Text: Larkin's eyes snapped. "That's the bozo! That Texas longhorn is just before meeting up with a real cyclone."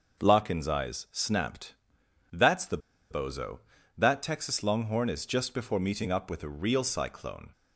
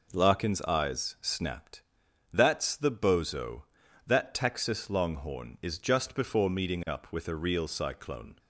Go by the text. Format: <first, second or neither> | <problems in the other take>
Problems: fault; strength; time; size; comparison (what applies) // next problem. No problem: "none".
second | starts louder than the rest; noticeable; until 1.2 s; 6 dB // pauses between "the" and "bozo"; slight; at 2.7 s; 0.32 s long